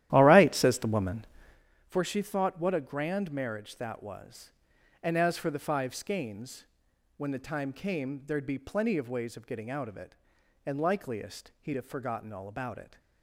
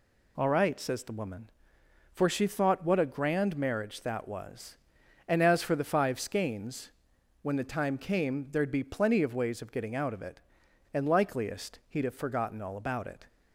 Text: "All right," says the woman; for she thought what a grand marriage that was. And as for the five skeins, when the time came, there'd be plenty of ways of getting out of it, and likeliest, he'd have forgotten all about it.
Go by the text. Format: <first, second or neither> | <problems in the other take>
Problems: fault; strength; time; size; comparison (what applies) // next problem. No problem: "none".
second | starts louder than the rest; strong; until 1.6 s; 13 dB